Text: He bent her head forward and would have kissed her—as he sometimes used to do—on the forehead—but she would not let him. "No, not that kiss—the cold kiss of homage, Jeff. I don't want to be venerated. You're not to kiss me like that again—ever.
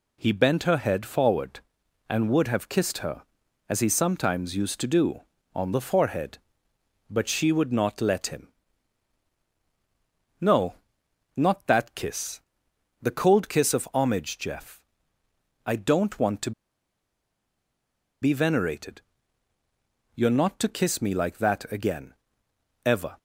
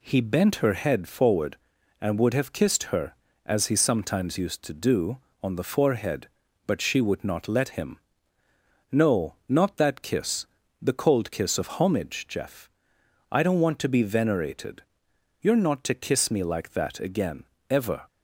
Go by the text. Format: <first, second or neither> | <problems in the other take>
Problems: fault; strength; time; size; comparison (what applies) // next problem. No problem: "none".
second | pauses between "to" and "be"; strong; at 16.5 s; 1.7 s long